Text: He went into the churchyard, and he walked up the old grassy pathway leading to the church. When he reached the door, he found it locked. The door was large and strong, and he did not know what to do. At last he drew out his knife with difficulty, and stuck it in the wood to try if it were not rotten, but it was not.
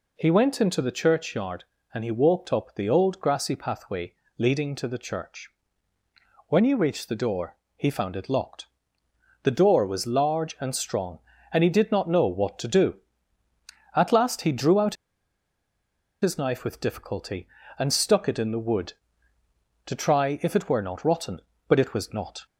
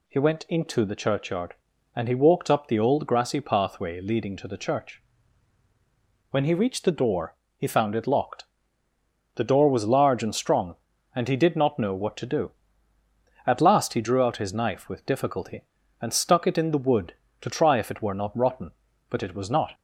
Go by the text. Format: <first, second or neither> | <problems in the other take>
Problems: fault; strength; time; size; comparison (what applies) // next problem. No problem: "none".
second | pauses between "pathway" and "leading"; slight; at 4.1 s; 0.24 s long // pauses between "out" and "his"; strong; at 14.9 s; 1.2 s long